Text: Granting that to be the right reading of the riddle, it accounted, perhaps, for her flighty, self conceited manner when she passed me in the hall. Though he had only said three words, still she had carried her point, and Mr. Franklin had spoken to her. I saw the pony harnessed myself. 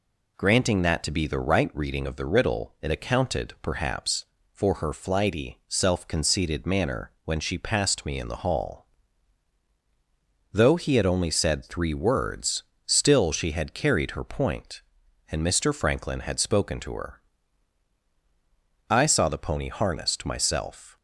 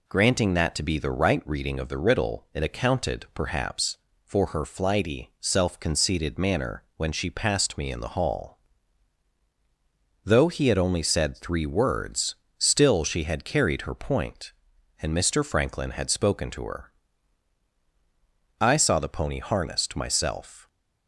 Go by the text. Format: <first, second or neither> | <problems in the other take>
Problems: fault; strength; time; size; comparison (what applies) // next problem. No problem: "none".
neither | none